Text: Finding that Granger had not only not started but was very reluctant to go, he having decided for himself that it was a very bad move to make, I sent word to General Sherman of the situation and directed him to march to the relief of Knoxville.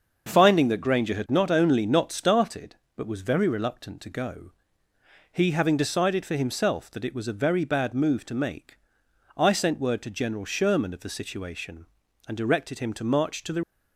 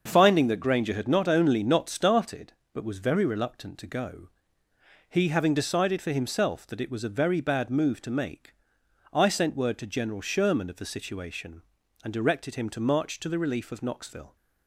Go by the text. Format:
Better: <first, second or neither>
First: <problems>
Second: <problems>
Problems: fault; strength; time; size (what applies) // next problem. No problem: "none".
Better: second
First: starts louder than the rest; until 1.3 s; 6.5 dB // stops before "relief of Knoxville"; at 13.6 s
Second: starts louder than the rest; until 1.0 s; 6.5 dB